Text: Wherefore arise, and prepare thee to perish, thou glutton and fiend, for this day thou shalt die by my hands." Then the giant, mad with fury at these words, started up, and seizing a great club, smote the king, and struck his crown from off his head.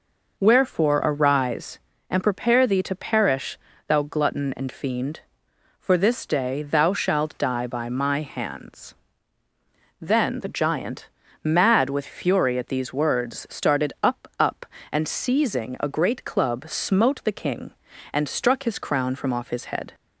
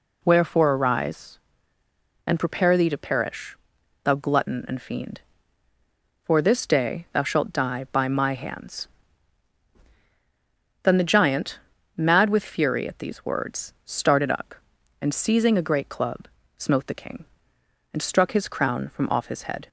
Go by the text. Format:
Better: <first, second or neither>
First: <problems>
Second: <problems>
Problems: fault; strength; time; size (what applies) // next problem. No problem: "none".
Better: second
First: says "up" twice; at 14.3 s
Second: none